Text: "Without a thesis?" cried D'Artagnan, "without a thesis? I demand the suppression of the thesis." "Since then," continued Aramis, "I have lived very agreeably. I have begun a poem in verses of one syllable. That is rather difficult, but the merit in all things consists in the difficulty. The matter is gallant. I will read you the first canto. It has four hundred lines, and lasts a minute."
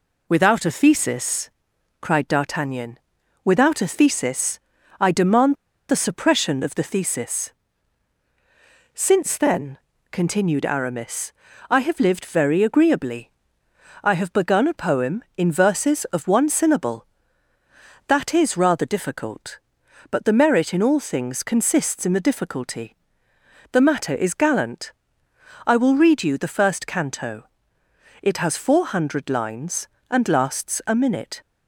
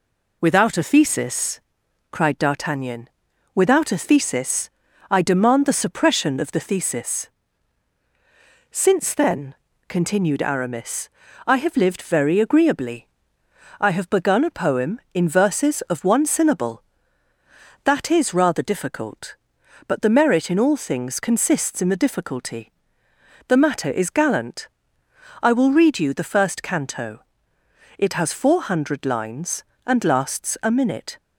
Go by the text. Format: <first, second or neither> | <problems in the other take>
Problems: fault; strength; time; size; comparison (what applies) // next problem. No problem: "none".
second | pauses between "demand" and "the"; slight; at 5.5 s; 0.34 s long